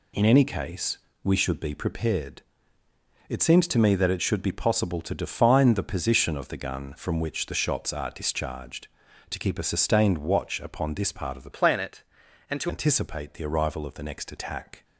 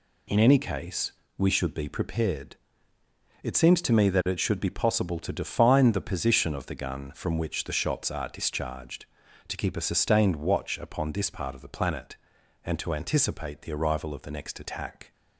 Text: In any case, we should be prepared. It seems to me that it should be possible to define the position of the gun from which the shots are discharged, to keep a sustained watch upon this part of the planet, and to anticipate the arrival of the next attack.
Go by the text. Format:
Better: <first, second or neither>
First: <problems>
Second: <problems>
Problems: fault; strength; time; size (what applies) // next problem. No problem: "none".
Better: second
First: changes voice from "planet" to "to"; from 11.5 to 12.6 s; 1.1 s long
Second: none